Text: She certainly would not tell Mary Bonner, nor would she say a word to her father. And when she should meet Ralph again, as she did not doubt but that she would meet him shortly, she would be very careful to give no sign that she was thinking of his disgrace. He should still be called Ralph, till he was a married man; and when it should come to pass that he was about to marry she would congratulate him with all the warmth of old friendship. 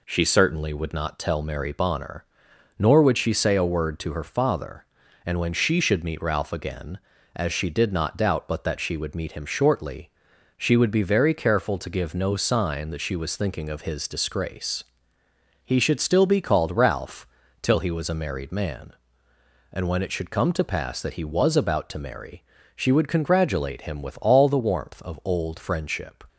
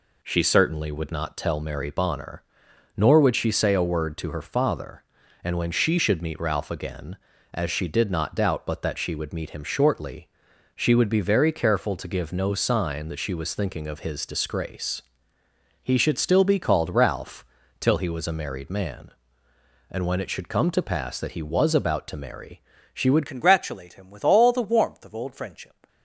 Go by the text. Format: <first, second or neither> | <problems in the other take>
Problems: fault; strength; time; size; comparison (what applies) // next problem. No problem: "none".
first | pauses between "marry" and "she"; slight; at 22.5 s; 0.32 s long; slight in the first // changes voice at "congratulate"; from 23.2 s on; 2.6 s long